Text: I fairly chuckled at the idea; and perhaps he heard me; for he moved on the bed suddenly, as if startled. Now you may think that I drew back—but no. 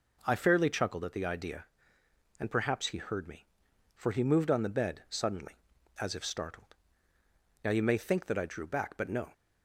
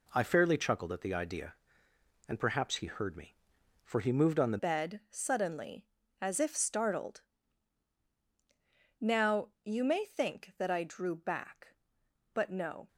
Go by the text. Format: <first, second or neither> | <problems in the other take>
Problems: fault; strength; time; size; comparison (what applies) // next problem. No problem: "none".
first | changes voice at "bed"; from 4.5 s on; 8.3 s long